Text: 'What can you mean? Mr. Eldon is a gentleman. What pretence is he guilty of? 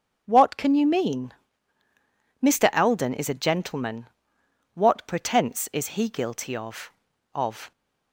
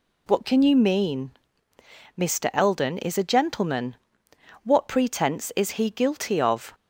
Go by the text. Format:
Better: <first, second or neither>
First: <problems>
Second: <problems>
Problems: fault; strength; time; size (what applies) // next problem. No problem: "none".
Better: second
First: starts louder than the rest; strong; until 1.2 s; 7.5 dB // says "of" twice; at 7.3 s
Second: none